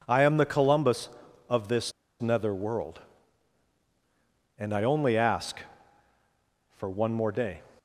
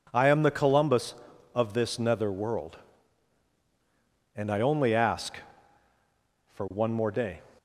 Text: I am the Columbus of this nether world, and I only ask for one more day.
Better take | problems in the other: second | pauses between "this" and "nether"; slight; at 1.9 s; 0.29 s long

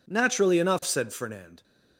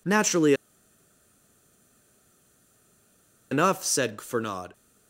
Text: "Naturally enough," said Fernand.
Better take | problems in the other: first | pauses between "Naturally" and "enough"; strong; at 0.5 s; 2.9 s long

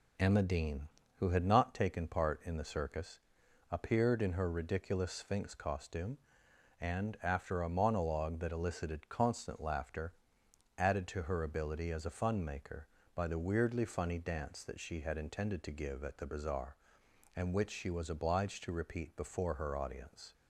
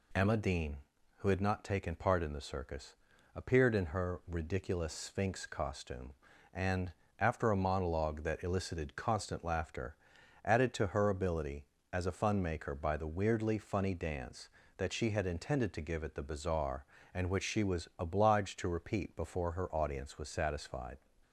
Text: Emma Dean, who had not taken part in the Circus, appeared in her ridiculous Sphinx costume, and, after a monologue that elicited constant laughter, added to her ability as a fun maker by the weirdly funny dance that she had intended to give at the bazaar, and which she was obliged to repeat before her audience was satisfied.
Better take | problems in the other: second | stops before "was satisfied"; at 20.3 s

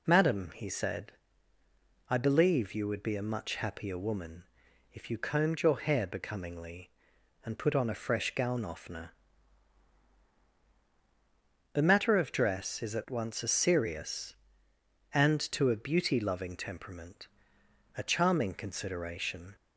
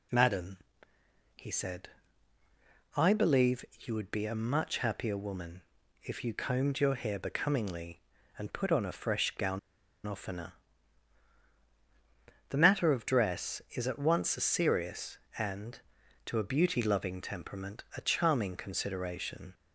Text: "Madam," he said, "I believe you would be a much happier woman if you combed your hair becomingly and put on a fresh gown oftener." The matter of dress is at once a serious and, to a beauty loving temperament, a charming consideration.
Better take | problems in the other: first | pauses between "woman" and "if"; at 5.6 s; 0.38 s long; noticeable in the first // pauses between "gown" and "oftener"; noticeable; at 9.5 s; 0.46 s long

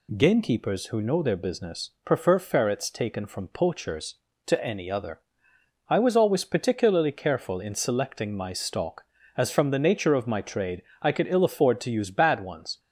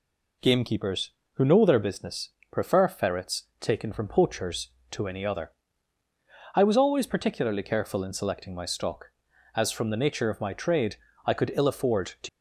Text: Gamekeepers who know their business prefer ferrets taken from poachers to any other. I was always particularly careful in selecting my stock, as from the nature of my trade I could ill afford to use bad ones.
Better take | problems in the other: first | pauses between "business" and "prefer"; slight; at 2.3 s; 0.22 s long // pauses between "trade" and "I"; slight; at 10.9 s; 0.30 s long; slight in the first // stops before "use bad ones"; at 12.2 s

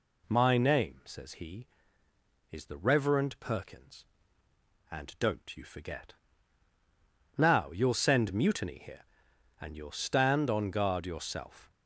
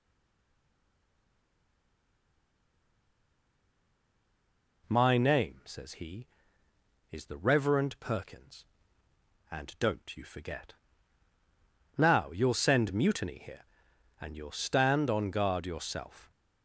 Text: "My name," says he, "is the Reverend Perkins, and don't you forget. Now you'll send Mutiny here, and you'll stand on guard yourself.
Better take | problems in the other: first | stays silent before the first word; strong; until 4.8 s; 4.8 s long

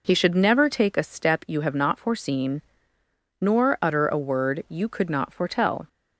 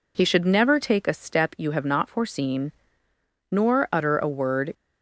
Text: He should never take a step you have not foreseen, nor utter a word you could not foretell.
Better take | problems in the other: first | stops before "you could not foretell"; at 4.7 s

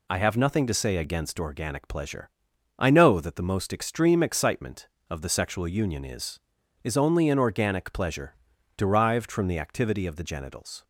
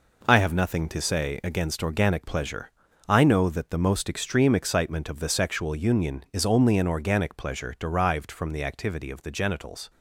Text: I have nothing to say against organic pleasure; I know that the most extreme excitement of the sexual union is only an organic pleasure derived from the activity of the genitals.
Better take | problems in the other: second | says "is" twice; at 6.8 s // pauses between "pleasure" and "derived"; at 8.3 s; 0.40 s long

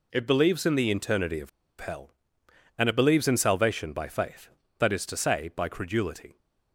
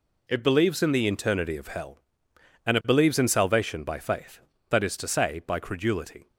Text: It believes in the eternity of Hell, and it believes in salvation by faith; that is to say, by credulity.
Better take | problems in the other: second | pauses between "of" and "Hell"; slight; at 1.4 s; 0.31 s long

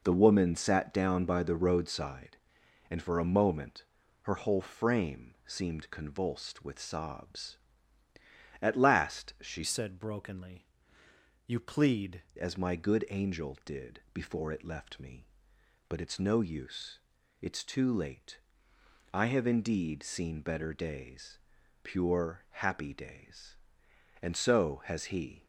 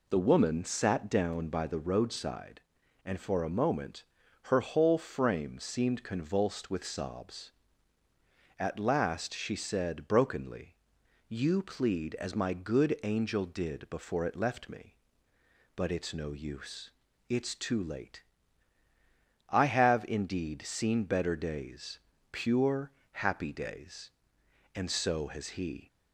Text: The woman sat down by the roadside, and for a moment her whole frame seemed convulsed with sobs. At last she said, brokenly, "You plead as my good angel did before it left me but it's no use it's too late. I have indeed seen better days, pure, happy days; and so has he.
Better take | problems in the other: second | pauses between "moment" and "her"; at 3.8 s; 0.38 s long; also in the second // changes voice from "said" to "plead"; from 9.6 to 12.2 s; 2.6 s long // pauses between "use" and "it's"; at 16.9 s; 0.40 s long; also in the second

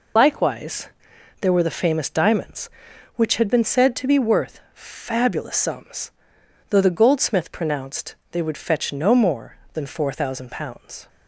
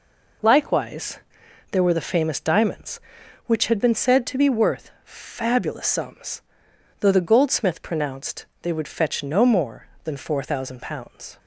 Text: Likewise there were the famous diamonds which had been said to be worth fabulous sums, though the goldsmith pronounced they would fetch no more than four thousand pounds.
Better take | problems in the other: second | loses the start of "Likewise"; at 0.1 s; 45 ms // pauses between "Likewise" and "there"; noticeable; at 0.8 s; 0.54 s long; noticeable in the second // pauses between "pronounced" and "they"; slight; at 8.1 s; 0.16 s long; slight in the second

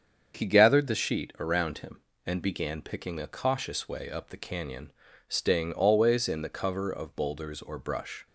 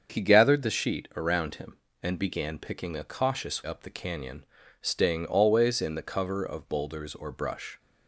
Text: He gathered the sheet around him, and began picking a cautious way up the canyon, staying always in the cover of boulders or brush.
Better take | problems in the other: first | starts louder than the rest; until 1.1 s; 7 dB; strong in the first // skips "way"; at 3.6 s

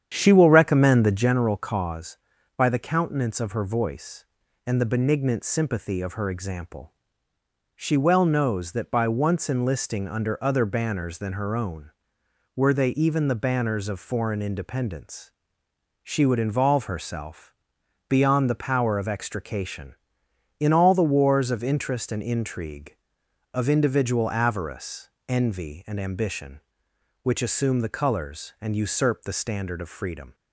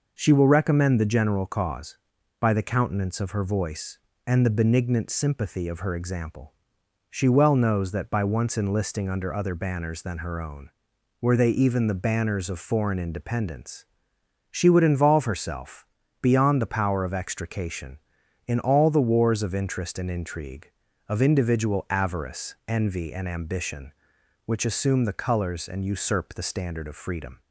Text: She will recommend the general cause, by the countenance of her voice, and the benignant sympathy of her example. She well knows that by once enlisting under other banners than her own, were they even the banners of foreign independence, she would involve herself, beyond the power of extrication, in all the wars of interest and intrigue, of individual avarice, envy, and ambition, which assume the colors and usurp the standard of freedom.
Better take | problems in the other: second | starts louder than the rest; strong; until 1.4 s; 9 dB

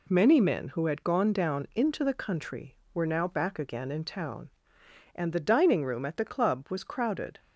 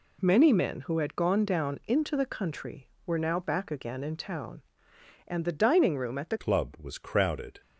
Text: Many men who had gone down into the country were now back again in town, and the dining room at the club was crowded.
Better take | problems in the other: first | changes voice at "club"; from 6.3 s on; 1.3 s long

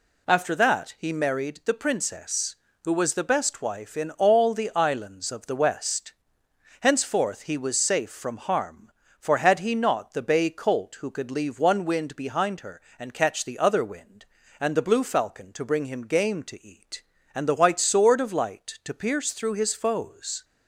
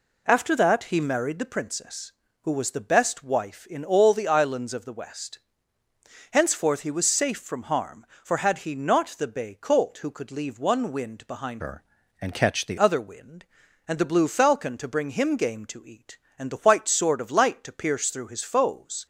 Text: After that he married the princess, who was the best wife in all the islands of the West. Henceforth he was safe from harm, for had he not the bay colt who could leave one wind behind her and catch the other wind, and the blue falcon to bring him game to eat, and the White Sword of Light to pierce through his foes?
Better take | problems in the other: first | changes voice from "her" to "the"; from 11.5 to 12.7 s; 1.2 s long

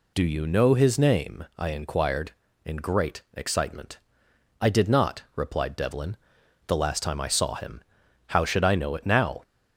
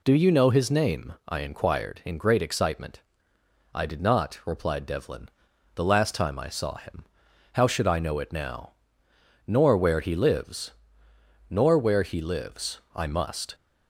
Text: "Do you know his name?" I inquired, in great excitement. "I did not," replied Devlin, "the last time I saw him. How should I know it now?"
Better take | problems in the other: first | goes on to say "Nor where he lives Nor where he lives I must"; strong; from 9.4 s on; 4.0 s long

